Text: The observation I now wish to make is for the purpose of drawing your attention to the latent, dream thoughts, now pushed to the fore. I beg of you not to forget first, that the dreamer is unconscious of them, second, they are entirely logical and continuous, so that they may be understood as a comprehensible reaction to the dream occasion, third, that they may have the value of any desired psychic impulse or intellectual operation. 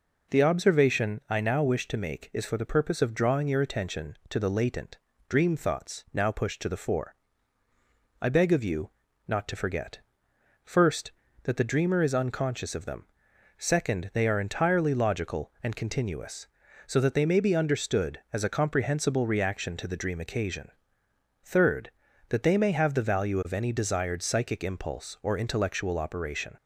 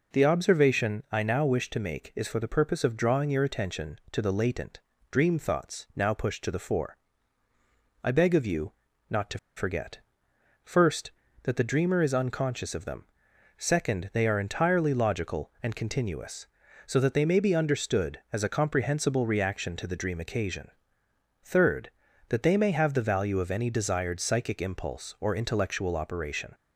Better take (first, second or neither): first